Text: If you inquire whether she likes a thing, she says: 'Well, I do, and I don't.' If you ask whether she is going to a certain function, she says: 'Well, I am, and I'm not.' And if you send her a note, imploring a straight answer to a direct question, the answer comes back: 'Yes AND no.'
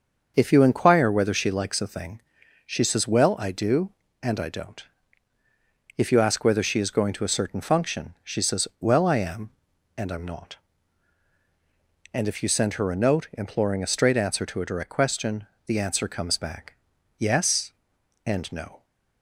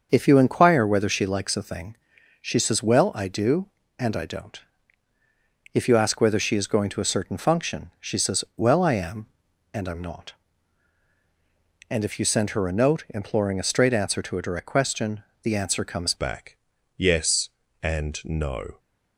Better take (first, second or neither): first